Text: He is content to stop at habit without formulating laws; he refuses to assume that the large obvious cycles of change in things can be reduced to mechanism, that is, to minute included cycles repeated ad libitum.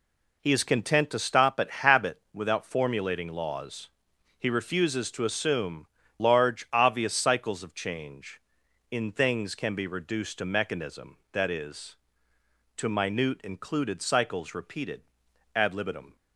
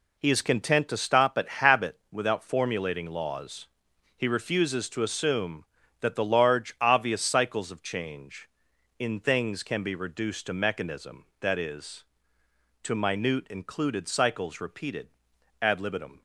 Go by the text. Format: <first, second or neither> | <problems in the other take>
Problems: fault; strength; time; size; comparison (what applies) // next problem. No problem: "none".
second | skips "that the"; at 6.0 s // pauses between "repeated" and "ad"; noticeable; at 15.0 s; 0.50 s long; noticeable in the second